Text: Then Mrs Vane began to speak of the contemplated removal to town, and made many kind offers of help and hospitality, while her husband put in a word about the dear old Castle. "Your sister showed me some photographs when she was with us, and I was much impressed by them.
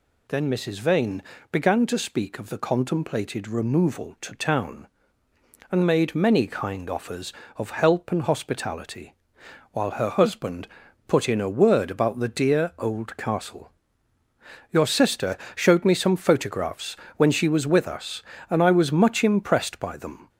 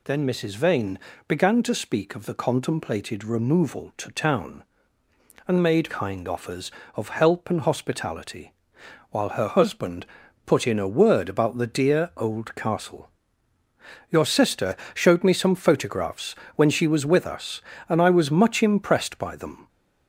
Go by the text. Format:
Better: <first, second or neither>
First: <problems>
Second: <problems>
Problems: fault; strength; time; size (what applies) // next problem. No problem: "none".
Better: first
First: pauses between "Vane" and "began"; slight; at 1.2 s; 0.30 s long // pauses between "husband" and "put"; at 10.6 s; 0.40 s long // pauses between "sister" and "showed"; slight; at 15.3 s; 0.18 s long // pauses between "photographs" and "when"; slight; at 16.9 s; 0.22 s long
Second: pauses between "Vane" and "began"; slight; at 0.9 s; 0.30 s long // skips "many"; at 5.8 s // pauses between "husband" and "put"; at 10.0 s; 0.40 s long // pauses between "sister" and "showed"; slight; at 14.7 s; 0.18 s long // pauses between "photographs" and "when"; slight; at 16.3 s; 0.22 s long